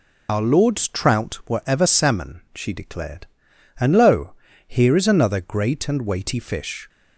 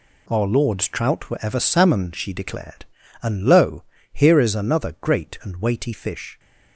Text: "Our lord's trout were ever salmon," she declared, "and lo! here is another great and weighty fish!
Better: second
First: loses the start of "Our"; at 0.2 s; 80 ms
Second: none

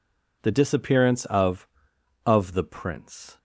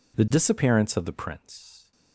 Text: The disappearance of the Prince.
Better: second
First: says "of" twice; at 2.2 s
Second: none

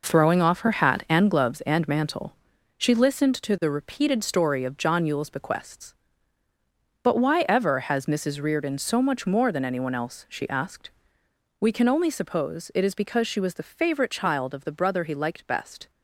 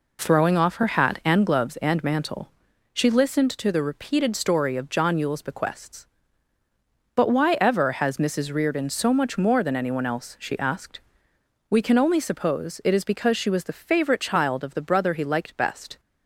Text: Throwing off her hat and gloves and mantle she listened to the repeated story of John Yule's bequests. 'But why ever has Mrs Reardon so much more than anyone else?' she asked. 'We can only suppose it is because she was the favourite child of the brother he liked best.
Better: second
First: gets quieter; strong; throughout; 8.5 dB // pauses between "mantle" and "she"; at 2.3 s; 0.40 s long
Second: pauses between "mantle" and "she"; at 2.5 s; 0.40 s long

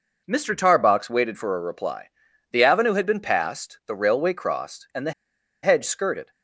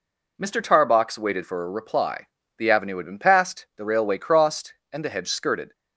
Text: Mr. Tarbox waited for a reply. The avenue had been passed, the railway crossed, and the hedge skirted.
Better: second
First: pauses between "the" and "hedge"; noticeable; at 5.1 s; 0.51 s long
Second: none

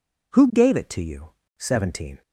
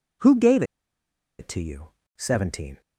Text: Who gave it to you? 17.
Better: first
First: none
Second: pauses between "gave" and "it"; noticeable; at 0.6 s; 0.75 s long

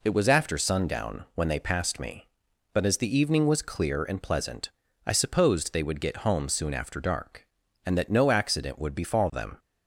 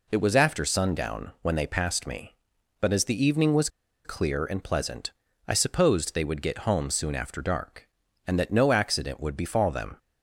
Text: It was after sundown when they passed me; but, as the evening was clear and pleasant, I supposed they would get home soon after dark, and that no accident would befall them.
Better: first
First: none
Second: pauses between "was" and "clear"; at 3.6 s; 0.37 s long

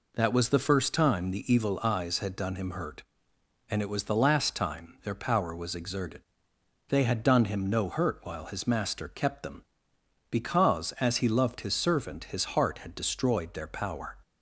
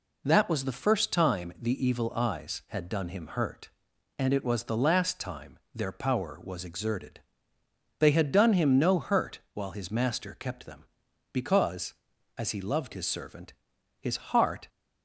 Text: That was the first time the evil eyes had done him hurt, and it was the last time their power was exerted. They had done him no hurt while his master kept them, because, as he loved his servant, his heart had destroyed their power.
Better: first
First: none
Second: pauses between "time" and "their"; slight; at 5.5 s; 0.16 s long // stops before "had destroyed their power"; at 14.6 s

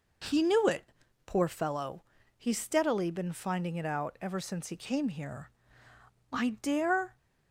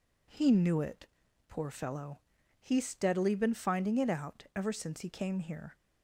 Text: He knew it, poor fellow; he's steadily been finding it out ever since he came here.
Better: second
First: goes on to say "I dare"; noticeable; from 6.3 s on; 0.86 s long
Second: none

